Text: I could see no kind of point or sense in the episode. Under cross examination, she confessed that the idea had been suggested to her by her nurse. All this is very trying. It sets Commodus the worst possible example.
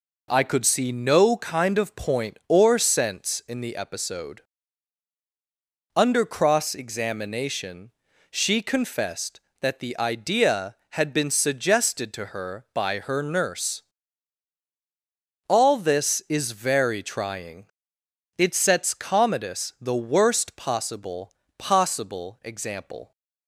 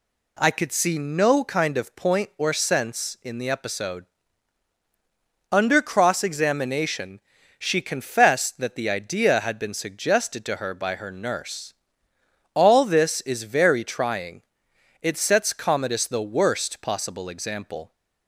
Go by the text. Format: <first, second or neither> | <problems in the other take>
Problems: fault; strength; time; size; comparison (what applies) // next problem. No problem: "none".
second | says "possible" twice; at 21.5 s